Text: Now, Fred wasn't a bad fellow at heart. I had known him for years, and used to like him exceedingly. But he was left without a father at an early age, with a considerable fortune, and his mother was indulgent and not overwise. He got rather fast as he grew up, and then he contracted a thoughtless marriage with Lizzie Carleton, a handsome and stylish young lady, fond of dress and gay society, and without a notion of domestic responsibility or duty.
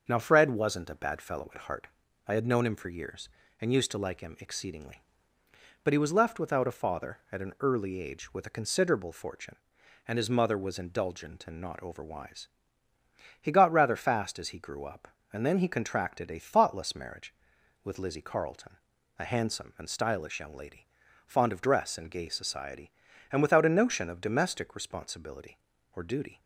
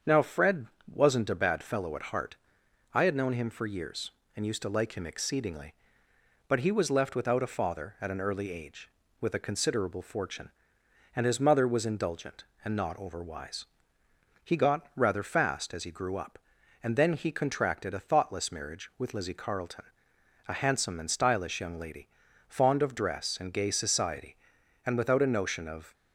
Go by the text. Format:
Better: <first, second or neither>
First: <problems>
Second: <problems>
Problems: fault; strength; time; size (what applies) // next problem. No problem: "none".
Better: first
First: starts louder than the rest; until 1.0 s; 6.5 dB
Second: starts louder than the rest; strong; until 1.3 s; 7 dB // pauses between "Fred" and "wasn't"; slight; at 0.6 s; 0.26 s long // stops before "domestic responsibility or duty"; at 25.9 s